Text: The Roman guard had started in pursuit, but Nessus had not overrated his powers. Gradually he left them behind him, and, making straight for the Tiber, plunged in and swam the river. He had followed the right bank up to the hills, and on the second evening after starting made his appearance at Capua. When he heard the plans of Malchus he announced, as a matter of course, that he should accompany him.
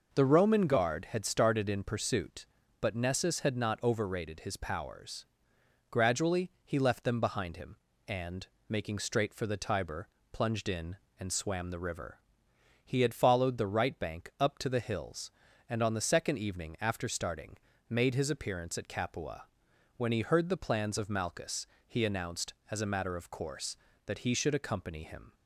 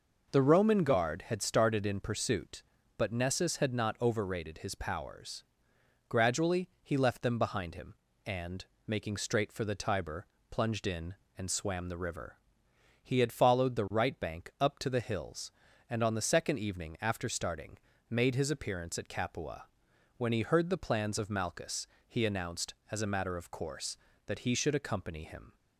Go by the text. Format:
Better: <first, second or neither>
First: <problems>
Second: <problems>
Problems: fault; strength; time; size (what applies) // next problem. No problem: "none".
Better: neither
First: pauses between "Gradually" and "he"; slight; at 6.4 s; 0.16 s long // pauses between "starting" and "made"; slight; at 17.5 s; 0.32 s long // pauses between "Malchus" and "he"; slight; at 21.6 s; 0.18 s long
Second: pauses between "Gradually" and "he"; slight; at 6.6 s; 0.16 s long // pauses between "starting" and "made"; slight; at 17.7 s; 0.32 s long // pauses between "Malchus" and "he"; slight; at 21.8 s; 0.18 s long